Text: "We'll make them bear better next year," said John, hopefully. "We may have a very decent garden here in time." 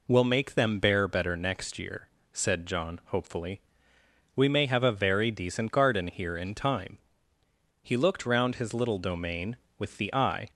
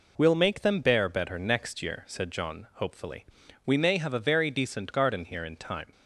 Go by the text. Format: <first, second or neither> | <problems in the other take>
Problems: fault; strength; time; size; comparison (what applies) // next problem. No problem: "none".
second | goes on to say "He looked round his little domain with the eye"; strong; from 7.8 s on; 2.6 s long